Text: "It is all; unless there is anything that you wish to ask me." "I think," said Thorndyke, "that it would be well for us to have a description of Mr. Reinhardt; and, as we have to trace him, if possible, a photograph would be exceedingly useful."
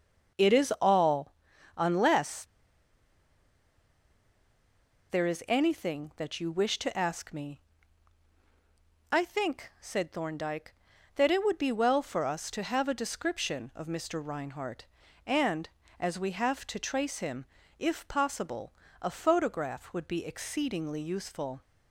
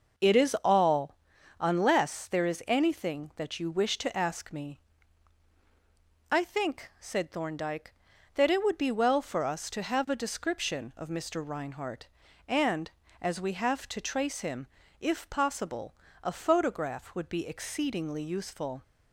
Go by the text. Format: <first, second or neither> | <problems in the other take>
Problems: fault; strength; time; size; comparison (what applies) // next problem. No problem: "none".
second | starts louder than the rest; noticeable; until 1.8 s; 6 dB; noticeable in the second // pauses between "unless" and "there"; strong; at 2.4 s; 2.6 s long